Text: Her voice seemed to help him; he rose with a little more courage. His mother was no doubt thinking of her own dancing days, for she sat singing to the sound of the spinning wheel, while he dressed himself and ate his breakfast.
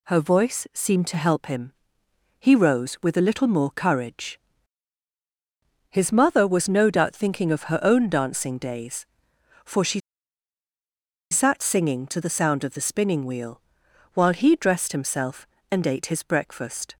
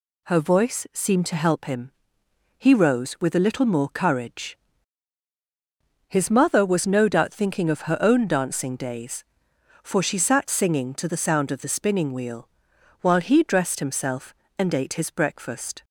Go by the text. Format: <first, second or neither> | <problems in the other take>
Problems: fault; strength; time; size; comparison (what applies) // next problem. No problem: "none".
second | pauses between "she" and "sat"; strong; at 9.9 s; 1.3 s long